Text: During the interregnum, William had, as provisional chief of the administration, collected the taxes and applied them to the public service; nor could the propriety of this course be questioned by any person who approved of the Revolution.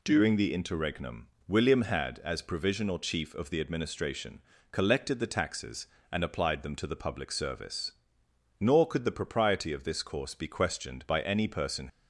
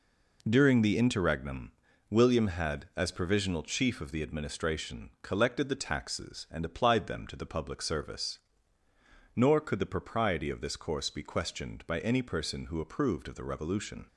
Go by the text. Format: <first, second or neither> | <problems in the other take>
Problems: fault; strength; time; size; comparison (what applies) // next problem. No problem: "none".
second | stops before "who approved of the Revolution"; at 11.8 s